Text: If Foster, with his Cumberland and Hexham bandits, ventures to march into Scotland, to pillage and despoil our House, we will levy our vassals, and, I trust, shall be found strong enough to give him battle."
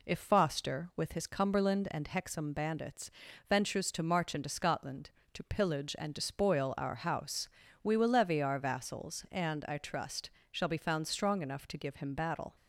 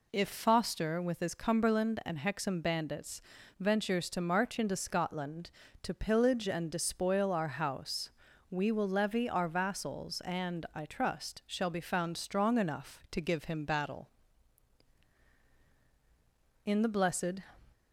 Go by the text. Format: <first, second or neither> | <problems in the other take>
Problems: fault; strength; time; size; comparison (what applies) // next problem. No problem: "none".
first | goes on to say "In the blessed"; noticeable; from 16.6 s on; 0.76 s long